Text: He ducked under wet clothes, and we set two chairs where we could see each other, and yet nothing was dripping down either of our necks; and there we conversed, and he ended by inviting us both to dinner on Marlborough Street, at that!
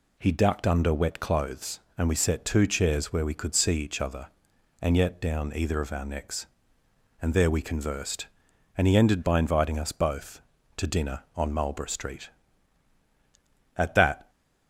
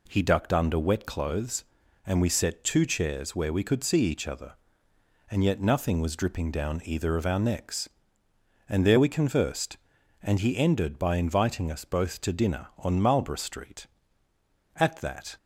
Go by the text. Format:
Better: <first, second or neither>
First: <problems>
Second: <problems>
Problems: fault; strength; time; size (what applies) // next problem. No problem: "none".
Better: second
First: skips "nothing was dripping"; at 5.2 s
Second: none